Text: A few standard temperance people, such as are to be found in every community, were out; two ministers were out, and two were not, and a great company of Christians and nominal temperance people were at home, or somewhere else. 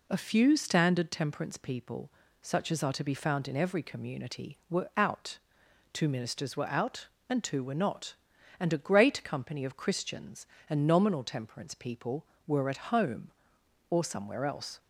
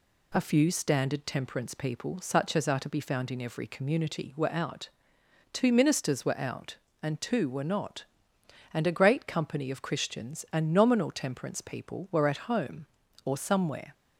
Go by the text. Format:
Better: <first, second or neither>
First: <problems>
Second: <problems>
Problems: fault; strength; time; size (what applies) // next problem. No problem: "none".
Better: first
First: none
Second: stops before "else"; at 13.9 s